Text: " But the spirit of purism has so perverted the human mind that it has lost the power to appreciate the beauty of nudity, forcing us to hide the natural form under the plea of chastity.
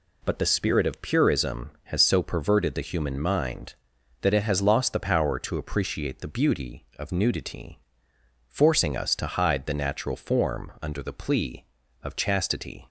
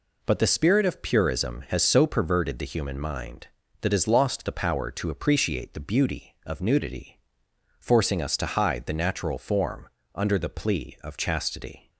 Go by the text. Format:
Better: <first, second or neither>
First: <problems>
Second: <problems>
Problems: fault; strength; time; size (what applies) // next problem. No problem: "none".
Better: first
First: none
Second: skips "it"; at 3.8 s // pauses between "form" and "under"; slight; at 9.8 s; 0.26 s long